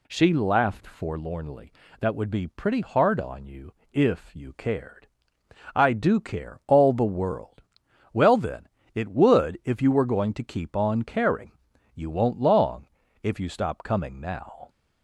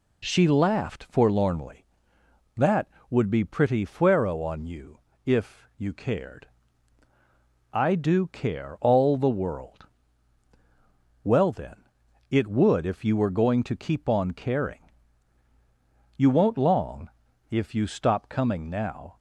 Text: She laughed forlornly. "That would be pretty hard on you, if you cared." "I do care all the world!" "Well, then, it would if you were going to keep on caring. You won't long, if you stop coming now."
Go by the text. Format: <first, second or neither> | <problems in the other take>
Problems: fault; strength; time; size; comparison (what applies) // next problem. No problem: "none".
first | says "fuero" for "hard"; at 3.8 s